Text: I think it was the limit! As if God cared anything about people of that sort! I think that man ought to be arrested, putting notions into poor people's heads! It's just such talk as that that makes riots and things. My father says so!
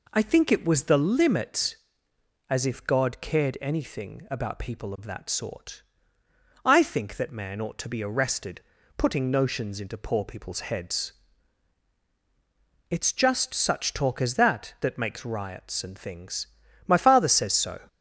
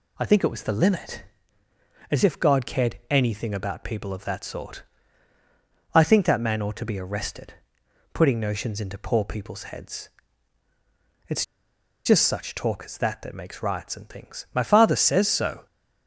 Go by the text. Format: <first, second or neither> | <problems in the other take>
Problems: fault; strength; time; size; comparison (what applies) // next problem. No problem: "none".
first | pauses between "It's" and "just"; noticeable; at 11.4 s; 0.60 s long